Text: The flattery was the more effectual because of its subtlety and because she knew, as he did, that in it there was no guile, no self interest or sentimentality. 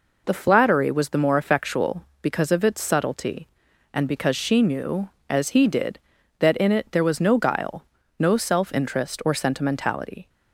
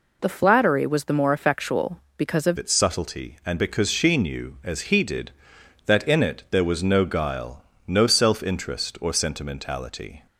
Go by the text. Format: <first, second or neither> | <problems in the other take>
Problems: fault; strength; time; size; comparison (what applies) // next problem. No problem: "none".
first | changes voice at "its"; from 2.5 s on; 7.7 s long